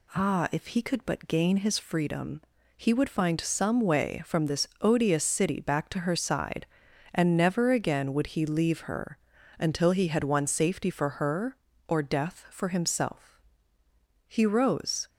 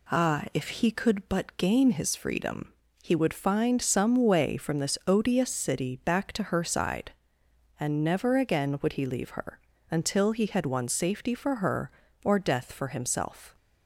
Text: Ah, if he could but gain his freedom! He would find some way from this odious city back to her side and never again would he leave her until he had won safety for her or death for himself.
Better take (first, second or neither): second